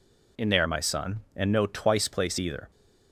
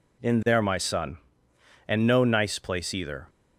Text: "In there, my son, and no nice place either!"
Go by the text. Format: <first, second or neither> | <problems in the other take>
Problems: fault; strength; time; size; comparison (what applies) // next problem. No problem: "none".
second | says "twice" for "nice"; at 1.6 s